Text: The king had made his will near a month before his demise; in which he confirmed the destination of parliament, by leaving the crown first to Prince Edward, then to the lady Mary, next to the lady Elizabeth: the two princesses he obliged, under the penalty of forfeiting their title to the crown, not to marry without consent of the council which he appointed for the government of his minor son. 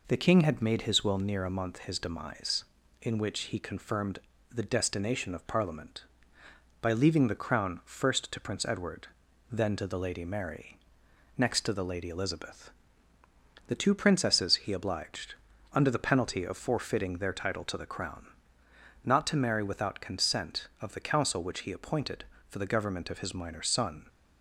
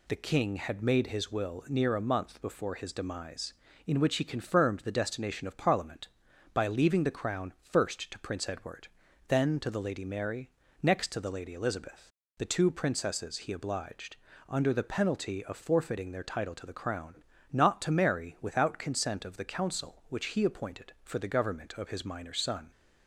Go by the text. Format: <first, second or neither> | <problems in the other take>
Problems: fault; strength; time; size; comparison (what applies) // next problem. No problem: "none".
second | skips "before"; at 1.7 s // pauses between "confirmed" and "the"; slight; at 4.1 s; 0.32 s long